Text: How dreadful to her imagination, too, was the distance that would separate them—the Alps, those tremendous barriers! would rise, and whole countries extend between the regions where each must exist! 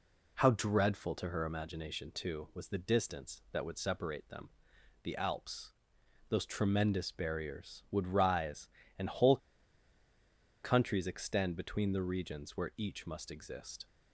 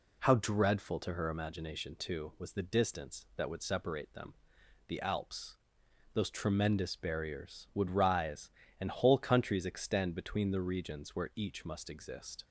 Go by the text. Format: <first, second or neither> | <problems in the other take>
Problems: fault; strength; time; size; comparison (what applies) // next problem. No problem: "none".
second | pauses between "whole" and "countries"; strong; at 9.3 s; 1.2 s long